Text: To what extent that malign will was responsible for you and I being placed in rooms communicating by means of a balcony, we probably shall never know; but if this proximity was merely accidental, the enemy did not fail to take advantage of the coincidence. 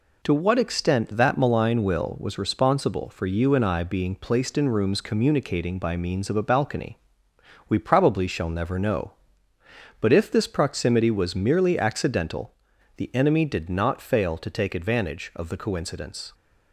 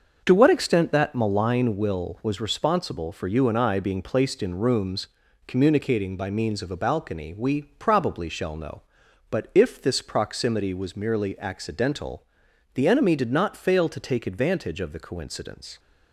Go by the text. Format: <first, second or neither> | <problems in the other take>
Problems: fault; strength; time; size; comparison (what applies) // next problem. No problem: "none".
first | starts louder than the rest; until 1.2 s; 6.5 dB // pauses between "rooms" and "communicating"; at 5.0 s; 0.40 s long // skips "never"; at 8.5 s